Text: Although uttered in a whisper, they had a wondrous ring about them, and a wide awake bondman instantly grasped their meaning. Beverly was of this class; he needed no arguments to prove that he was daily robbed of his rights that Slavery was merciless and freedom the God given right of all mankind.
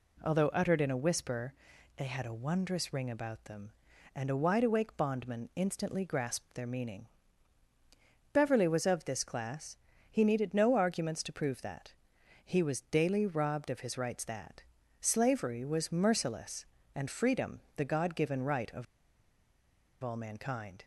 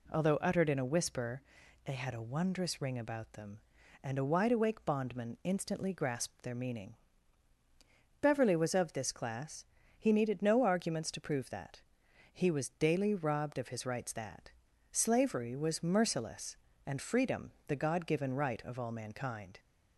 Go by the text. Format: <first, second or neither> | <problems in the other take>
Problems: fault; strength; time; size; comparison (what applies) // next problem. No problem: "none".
second | pauses between "that" and "he"; noticeable; at 11.9 s; 0.52 s long; noticeable in the second // pauses between "that" and "Slavery"; slight; at 14.6 s; 0.36 s long; also in the second // pauses between "freedom" and "the"; slight; at 17.6 s; 0.16 s long; slight in the second // pauses between "of" and "all"; at 18.8 s; 1.1 s long